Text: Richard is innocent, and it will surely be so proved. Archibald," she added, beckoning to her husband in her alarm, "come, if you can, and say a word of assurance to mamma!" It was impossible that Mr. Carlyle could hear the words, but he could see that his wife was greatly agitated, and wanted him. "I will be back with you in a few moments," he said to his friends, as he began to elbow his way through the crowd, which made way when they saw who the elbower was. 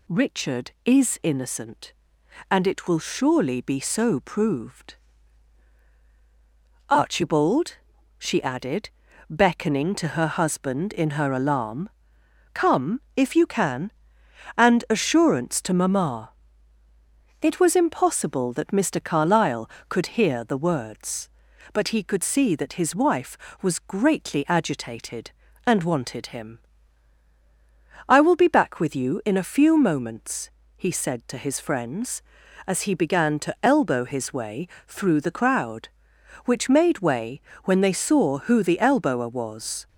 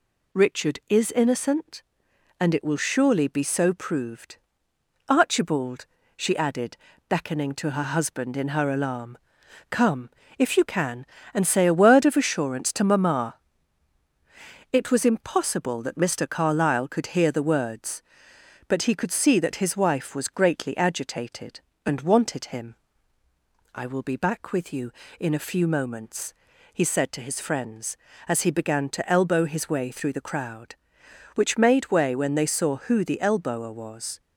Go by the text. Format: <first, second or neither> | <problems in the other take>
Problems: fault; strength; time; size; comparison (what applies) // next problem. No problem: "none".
second | skips "say a word of"; at 14.8 s // pauses between "way" and "through"; slight; at 34.6 s; 0.20 s long // pauses between "way" and "when"; slight; at 37.4 s; 0.24 s long